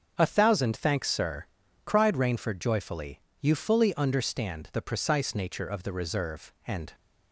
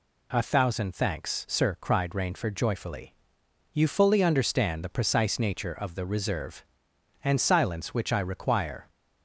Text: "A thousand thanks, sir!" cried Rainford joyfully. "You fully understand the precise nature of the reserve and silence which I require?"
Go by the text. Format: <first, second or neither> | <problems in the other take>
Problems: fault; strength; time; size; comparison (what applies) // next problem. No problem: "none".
second | starts louder than the rest; until 1.1 s; 7 dB // stops before "silence which I require"; at 6.9 s